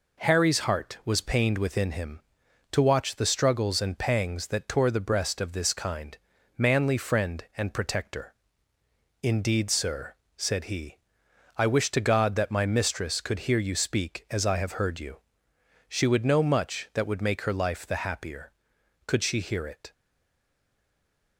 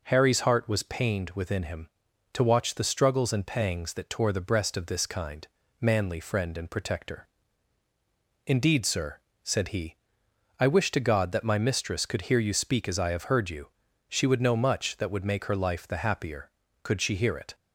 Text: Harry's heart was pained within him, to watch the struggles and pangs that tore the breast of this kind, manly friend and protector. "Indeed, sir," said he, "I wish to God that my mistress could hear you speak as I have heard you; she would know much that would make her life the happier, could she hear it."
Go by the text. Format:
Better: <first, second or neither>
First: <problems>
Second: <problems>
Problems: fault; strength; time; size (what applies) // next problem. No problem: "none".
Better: second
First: stays silent after the last word; noticeable; from 19.9 s on; 1.4 s long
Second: none